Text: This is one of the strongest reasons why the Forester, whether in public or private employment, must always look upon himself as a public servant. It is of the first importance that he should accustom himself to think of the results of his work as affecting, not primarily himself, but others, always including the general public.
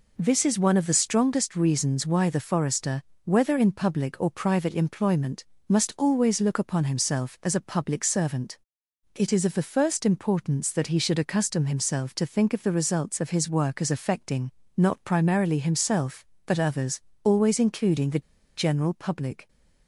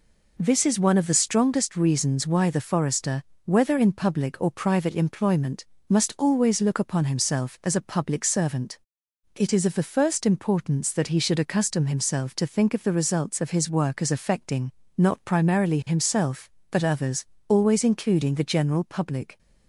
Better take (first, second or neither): second